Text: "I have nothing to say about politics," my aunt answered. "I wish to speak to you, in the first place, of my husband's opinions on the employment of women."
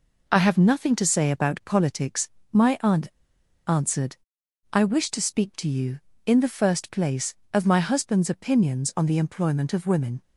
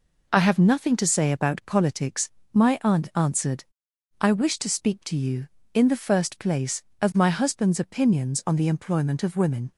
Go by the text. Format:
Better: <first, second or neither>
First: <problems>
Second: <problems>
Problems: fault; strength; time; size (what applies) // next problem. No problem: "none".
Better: second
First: pauses between "aunt" and "answered"; noticeable; at 3.0 s; 0.61 s long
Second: none